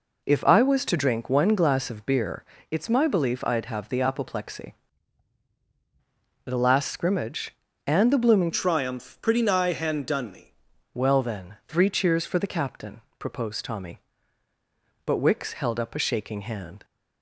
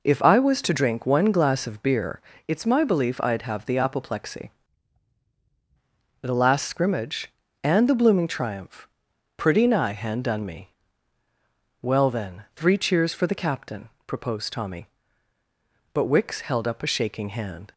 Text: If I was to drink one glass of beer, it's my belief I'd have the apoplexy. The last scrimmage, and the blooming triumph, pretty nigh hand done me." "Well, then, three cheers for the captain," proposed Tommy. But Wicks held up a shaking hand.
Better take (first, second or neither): second